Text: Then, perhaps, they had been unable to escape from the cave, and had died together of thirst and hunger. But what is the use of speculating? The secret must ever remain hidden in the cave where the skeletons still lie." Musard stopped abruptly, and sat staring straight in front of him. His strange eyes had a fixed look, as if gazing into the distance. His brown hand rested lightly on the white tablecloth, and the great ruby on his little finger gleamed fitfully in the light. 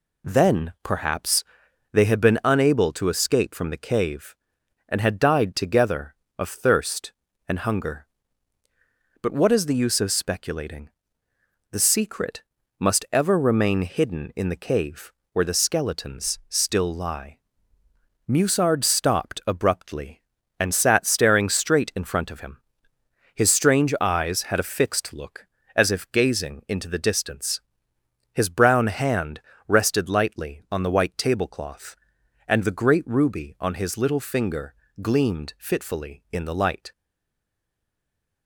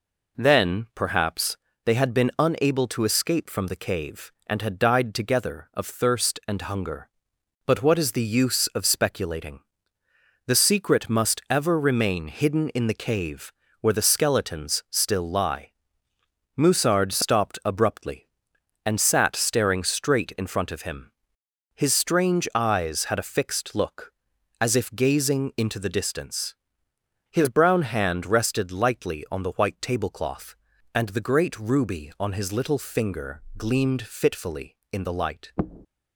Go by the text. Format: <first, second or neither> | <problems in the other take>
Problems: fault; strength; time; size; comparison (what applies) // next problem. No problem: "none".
second | pauses between "secret" and "must"; at 12.4 s; 0.38 s long // pauses between "cave" and "where"; slight; at 15.1 s; 0.20 s long; slight in the second // pauses between "hand" and "rested"; slight; at 29.4 s; 0.26 s long // pauses between "finger" and "gleamed"; slight; at 34.7 s; 0.28 s long; slight in the second // stays silent after the last word; noticeable; from 36.9 s on; 1.5 s long